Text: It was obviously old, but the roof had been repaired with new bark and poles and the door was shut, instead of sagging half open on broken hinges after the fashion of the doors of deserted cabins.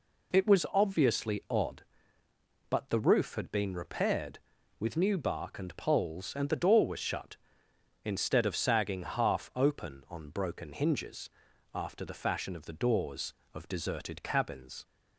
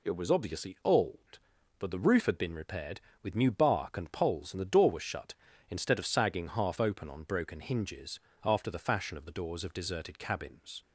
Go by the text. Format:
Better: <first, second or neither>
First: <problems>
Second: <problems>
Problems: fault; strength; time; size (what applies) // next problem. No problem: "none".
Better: second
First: says "odd" for "old"; at 1.4 s // pauses between "hinges" and "after"; noticeable; at 11.2 s; 0.46 s long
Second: pauses between "hinges" and "after"; slight; at 8.1 s; 0.24 s long